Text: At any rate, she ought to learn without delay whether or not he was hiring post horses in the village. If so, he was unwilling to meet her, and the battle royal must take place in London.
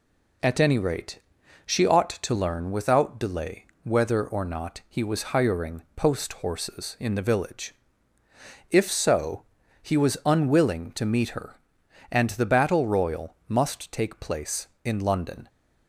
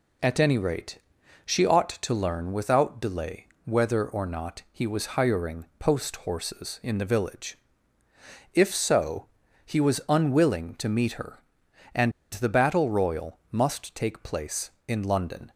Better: first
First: pauses between "delay" and "whether"; slight; at 3.6 s; 0.20 s long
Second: pauses between "delay" and "whether"; slight; at 3.4 s; 0.20 s long // pauses between "and" and "the"; slight; at 12.1 s; 0.21 s long

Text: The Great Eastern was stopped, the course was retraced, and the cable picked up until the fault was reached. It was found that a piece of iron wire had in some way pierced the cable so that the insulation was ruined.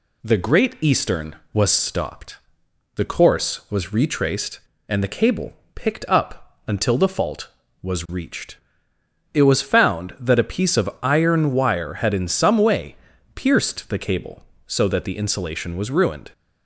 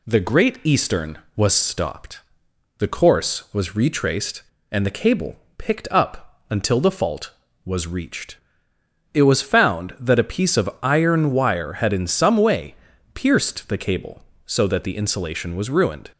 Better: neither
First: pauses between "cable" and "picked"; slight; at 5.5 s; 0.20 s long // pauses between "way" and "pierced"; at 12.9 s; 0.40 s long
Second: pauses between "cable" and "picked"; slight; at 5.3 s; 0.20 s long // pauses between "way" and "pierced"; at 12.7 s; 0.40 s long

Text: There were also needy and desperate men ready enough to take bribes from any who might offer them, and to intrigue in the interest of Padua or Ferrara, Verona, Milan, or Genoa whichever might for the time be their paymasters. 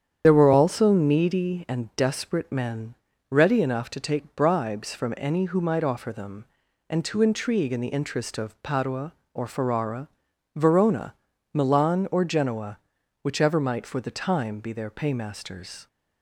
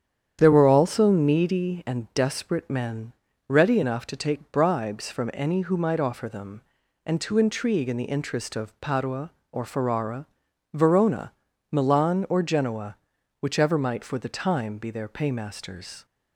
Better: second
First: loses the start of "There"; at 0.2 s; 40 ms // starts louder than the rest; strong; until 1.2 s; 9 dB // pauses between "men" and "ready"; at 2.9 s; 0.38 s long // pauses between "Genoa" and "whichever"; at 12.7 s; 0.44 s long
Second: starts louder than the rest; strong; until 1.4 s; 9 dB // pauses between "men" and "ready"; at 3.1 s; 0.38 s long // pauses between "Genoa" and "whichever"; at 12.9 s; 0.44 s long

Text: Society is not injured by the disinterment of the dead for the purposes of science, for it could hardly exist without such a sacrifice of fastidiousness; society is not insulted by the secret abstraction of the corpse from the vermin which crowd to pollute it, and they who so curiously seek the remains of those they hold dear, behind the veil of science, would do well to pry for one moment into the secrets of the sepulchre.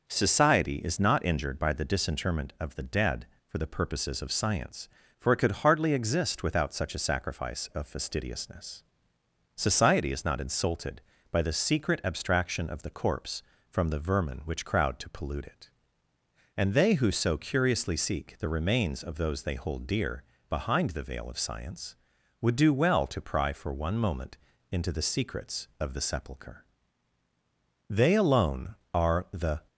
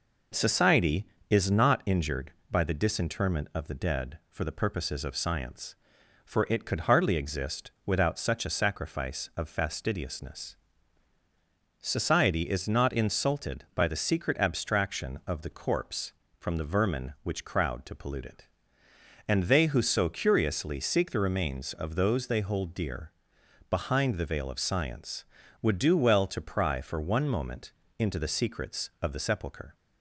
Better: second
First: starts louder than the rest; until 1.1 s; 6 dB // pauses between "moment" and "into"; slight; at 24.3 s; 0.34 s long // goes on to say "They alone are the"; strong; from 27.9 s on; 1.7 s long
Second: pauses between "moment" and "into"; slight; at 27.7 s; 0.28 s long

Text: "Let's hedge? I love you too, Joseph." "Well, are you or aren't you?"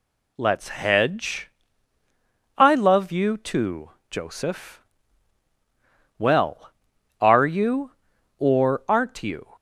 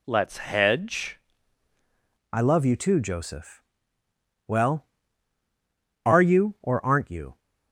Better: first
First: none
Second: changes voice at "I"; from 2.3 s on; 5.0 s long

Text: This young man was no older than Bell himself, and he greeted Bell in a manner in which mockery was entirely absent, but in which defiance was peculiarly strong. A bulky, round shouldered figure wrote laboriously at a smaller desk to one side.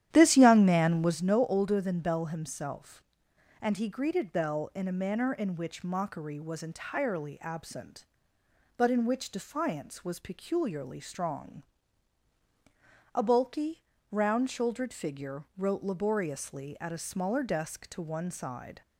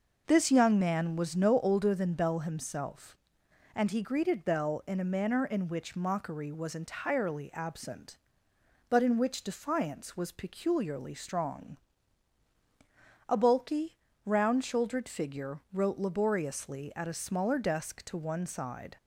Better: second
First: starts louder than the rest; strong; until 1.2 s; 11.5 dB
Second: none

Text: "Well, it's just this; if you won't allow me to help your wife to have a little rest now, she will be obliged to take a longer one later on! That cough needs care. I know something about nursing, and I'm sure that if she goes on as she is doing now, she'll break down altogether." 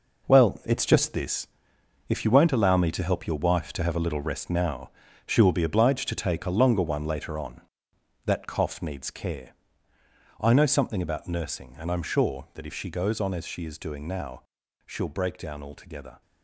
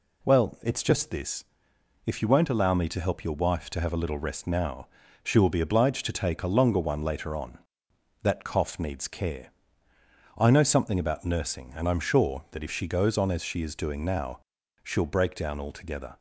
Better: second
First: gets quieter; strong; throughout; 8.5 dB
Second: none

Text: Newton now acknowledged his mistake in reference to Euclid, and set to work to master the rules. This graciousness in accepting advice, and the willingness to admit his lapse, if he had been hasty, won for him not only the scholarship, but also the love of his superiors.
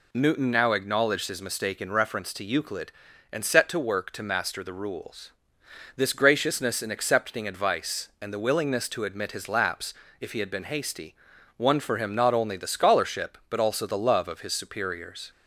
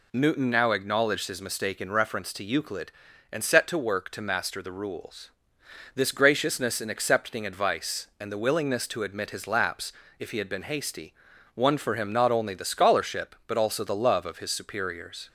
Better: neither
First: none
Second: none

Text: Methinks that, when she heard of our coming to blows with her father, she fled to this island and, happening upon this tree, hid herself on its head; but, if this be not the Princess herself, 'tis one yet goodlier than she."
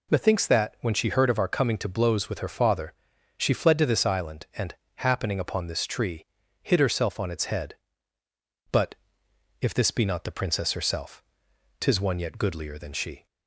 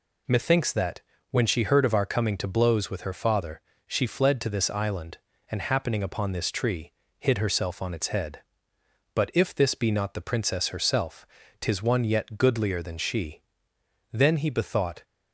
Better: first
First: none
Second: goes on to say "Then he bethought"; noticeable; from 14.1 s on; 0.90 s long

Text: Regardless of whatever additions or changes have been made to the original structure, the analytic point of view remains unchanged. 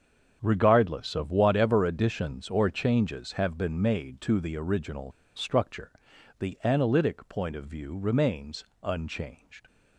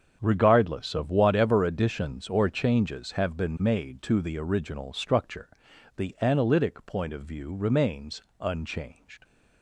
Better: second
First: starts louder than the rest; strong; until 1.4 s; 7.5 dB // pauses between "original" and "structure"; slight; at 5.1 s; 0.25 s long // pauses between "remains" and "unchanged"; slight; at 8.6 s; 0.16 s long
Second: starts louder than the rest; strong; until 1.2 s; 7.5 dB // pauses between "remains" and "unchanged"; slight; at 8.2 s; 0.16 s long

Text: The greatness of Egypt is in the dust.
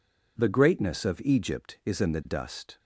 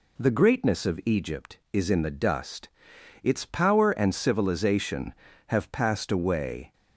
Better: first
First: none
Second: goes on to say "Its power and civilization have passed away"; strong; from 3.2 s on; 3.5 s long

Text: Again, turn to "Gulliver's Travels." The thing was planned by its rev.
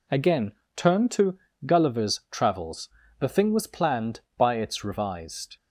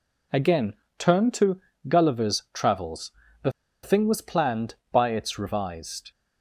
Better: first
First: pauses between "to" and "Gulliver's"; slight; at 1.3 s; 0.28 s long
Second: pauses between "to" and "Gulliver's"; slight; at 1.5 s; 0.28 s long // pauses between "The" and "thing"; slight; at 3.5 s; 0.32 s long

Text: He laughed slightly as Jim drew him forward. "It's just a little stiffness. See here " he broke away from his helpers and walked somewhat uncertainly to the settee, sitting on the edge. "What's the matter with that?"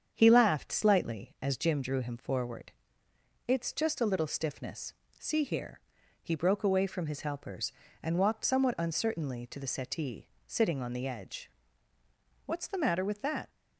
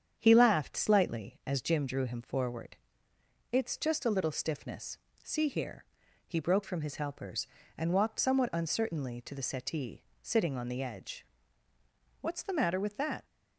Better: first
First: starts louder than the rest; strong; until 1.1 s; 7.5 dB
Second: starts louder than the rest; strong; until 1.1 s; 8 dB // skips "away"; at 6.6 s

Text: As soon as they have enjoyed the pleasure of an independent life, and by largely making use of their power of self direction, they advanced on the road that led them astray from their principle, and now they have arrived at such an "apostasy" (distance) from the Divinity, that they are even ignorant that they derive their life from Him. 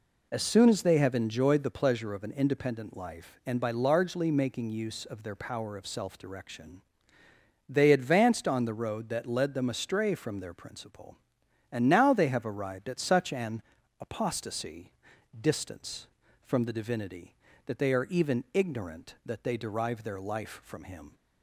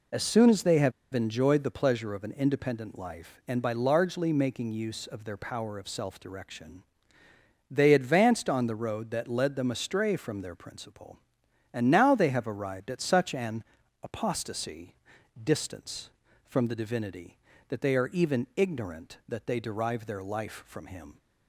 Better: first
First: pauses between "an" and "apostasy"; at 13.6 s; 0.38 s long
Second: pauses between "have" and "enjoyed"; slight; at 0.9 s; 0.22 s long // pauses between "an" and "apostasy"; at 13.6 s; 0.40 s long

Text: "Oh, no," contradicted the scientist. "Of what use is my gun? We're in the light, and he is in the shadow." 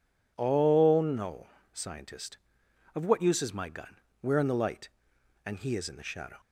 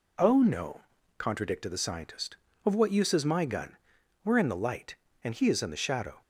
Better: second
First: skips "contradicted the"; at 1.5 s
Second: none

